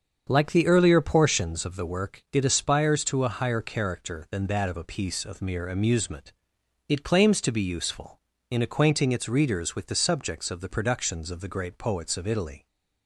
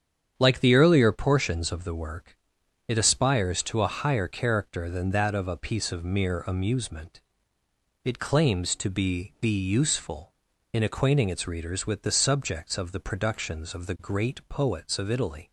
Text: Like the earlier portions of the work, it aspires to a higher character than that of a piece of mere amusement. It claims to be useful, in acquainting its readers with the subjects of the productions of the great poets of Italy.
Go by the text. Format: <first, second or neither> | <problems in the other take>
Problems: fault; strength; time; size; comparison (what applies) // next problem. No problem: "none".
first | starts louder than the rest; strong; until 1.3 s; 8.5 dB; also in the first // says "be" twice; at 9.3 s